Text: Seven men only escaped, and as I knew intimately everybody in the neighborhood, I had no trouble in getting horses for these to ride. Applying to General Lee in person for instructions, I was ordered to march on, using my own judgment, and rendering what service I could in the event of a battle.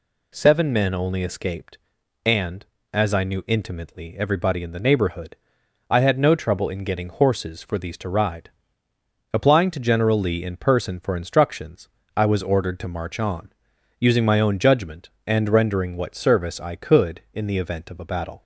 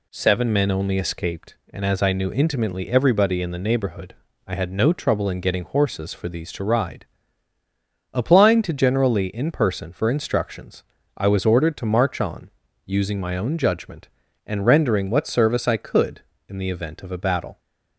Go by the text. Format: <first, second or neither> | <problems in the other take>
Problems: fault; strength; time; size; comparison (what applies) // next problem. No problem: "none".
neither | none